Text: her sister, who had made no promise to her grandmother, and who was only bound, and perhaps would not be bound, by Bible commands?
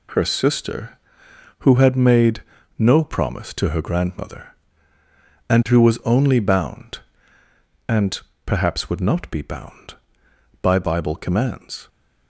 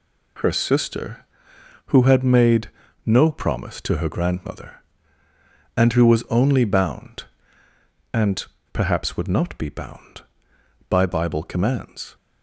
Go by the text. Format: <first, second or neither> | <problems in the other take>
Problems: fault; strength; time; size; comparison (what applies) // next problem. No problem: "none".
neither | pauses between "made" and "no"; slight; the same in both // pauses between "and" and "perhaps"; slight; the same in both